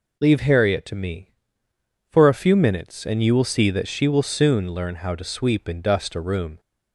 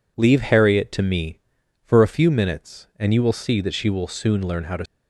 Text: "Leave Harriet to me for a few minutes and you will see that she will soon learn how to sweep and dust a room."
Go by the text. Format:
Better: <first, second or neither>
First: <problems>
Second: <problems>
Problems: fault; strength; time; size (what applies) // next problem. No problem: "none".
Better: first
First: none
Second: stops before "sweep and dust a room"; at 4.8 s